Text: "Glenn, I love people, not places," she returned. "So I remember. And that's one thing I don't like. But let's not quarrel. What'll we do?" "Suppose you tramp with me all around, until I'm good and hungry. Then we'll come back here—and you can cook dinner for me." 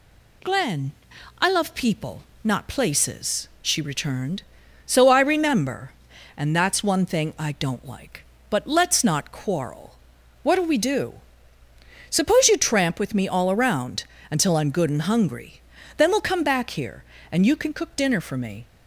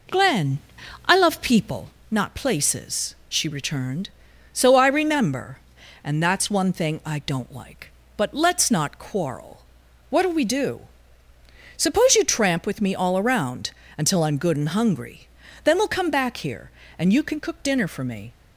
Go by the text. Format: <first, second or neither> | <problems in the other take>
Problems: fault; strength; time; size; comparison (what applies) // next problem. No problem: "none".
first | starts louder than the rest; noticeable; until 2.0 s; 4.5 dB